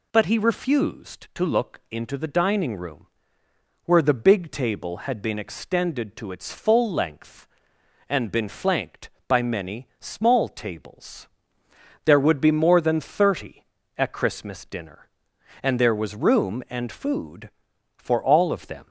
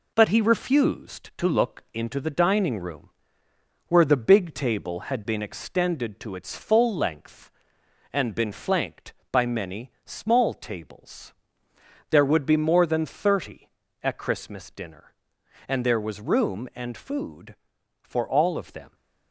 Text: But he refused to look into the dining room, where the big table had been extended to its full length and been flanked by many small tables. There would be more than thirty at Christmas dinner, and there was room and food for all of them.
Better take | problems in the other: first | gets quieter; throughout; 3.5 dB // pauses between "many" and "small"; slight; at 9.8 s; 0.16 s long

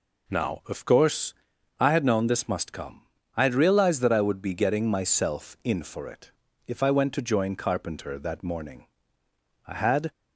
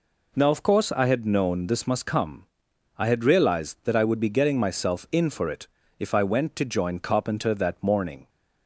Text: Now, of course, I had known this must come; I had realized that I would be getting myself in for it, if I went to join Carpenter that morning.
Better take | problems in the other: second | goes on to say "I had"; slight; from 9.6 s on; 0.42 s long

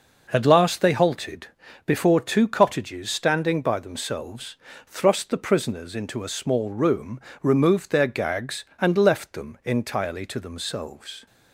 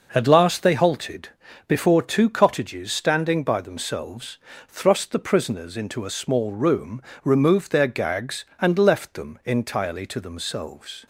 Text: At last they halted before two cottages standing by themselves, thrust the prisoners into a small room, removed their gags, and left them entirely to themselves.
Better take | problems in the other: neither | pauses between "halted" and "before"; the same in both

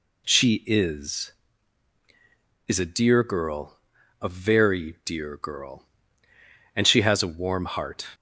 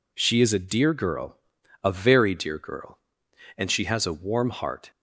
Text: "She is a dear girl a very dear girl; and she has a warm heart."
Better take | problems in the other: second | says "is" twice; at 2.6 s // pauses between "girl" and "a"; noticeable; at 3.7 s; 0.46 s long; noticeable in the second

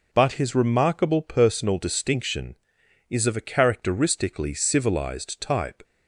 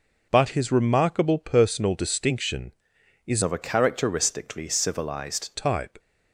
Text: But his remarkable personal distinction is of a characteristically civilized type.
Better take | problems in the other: first | changes voice from "of" to "civilized"; from 3.4 to 5.5 s; 2.1 s long

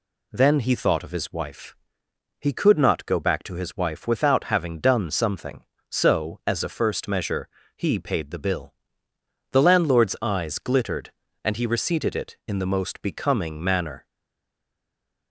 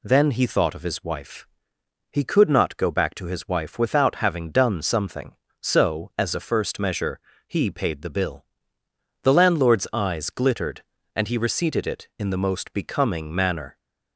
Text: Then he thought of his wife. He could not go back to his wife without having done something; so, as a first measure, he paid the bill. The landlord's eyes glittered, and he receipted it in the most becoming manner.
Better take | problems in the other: second | stays silent after the last word; noticeable; from 14.0 s on; 1.3 s long

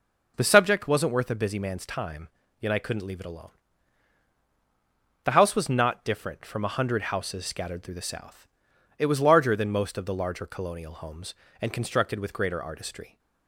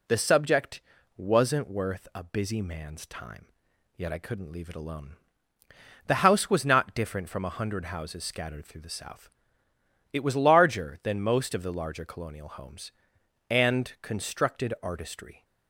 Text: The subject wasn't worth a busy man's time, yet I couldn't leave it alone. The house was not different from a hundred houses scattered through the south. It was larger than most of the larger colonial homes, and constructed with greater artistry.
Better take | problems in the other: first | pauses between "subject" and "wasn't"; slight; at 0.8 s; 0.34 s long // skips "with greater"; at 14.7 s

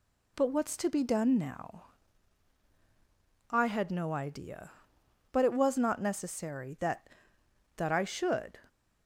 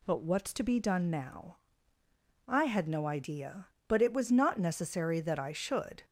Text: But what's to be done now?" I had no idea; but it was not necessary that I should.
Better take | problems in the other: second | says "that" twice; at 7.7 s

